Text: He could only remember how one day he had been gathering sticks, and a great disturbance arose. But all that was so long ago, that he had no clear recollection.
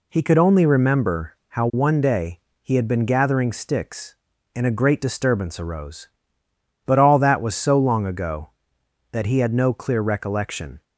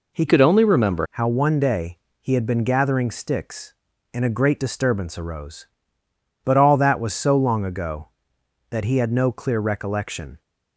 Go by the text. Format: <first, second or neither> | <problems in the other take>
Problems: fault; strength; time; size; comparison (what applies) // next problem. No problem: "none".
first | changes voice from "could" to "remember"; from 0.2 to 1.0 s; 0.8 s long // pauses between "day" and "he"; slight; at 1.9 s; 0.22 s long; slight in the first